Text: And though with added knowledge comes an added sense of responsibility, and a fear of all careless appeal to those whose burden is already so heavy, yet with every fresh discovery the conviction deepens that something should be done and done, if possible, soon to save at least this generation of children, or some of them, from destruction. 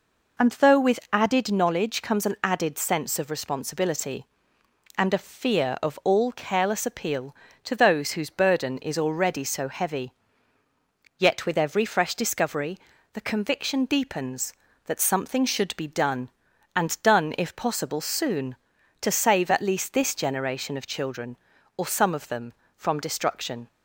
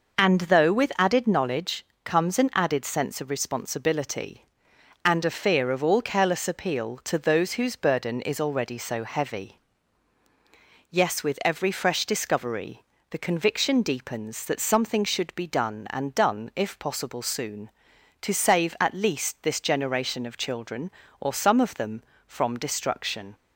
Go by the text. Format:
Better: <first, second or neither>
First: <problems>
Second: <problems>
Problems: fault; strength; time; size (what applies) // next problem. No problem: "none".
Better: first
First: pauses between "discovery" and "the"; slight; at 12.7 s; 0.36 s long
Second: pauses between "knowledge" and "comes"; slight; at 1.8 s; 0.18 s long // says "yes" for "yet"; at 10.9 s // pauses between "discovery" and "the"; slight; at 12.8 s; 0.26 s long